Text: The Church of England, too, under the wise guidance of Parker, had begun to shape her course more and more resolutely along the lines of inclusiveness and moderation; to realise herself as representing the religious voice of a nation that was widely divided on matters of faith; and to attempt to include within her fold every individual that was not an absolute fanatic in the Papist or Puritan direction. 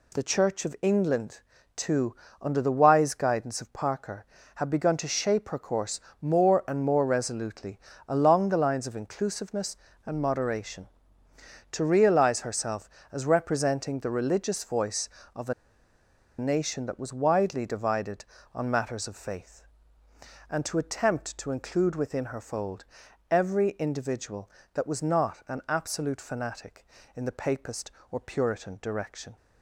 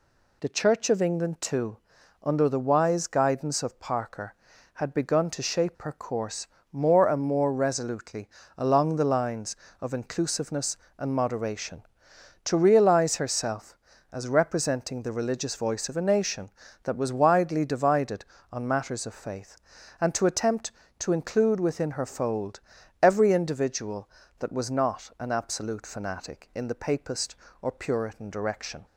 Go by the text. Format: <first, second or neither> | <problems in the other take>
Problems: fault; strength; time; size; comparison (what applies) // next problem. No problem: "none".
second | pauses between "course" and "more"; slight; at 5.9 s; 0.22 s long; slight in the second // pauses between "resolutely" and "along"; slight; at 7.7 s; 0.28 s long; slight in the second // pauses between "a" and "nation"; noticeable; at 15.5 s; 0.86 s long // pauses between "fold" and "every"; noticeable; at 22.8 s; 0.46 s long; also in the second